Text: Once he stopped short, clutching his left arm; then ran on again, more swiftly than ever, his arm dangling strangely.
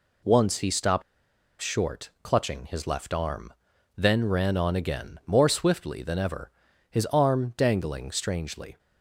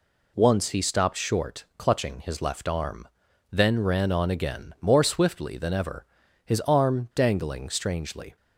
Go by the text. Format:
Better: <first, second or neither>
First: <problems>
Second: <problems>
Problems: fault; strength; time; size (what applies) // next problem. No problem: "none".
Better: second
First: pauses between "stopped" and "short"; noticeable; at 1.0 s; 0.59 s long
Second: none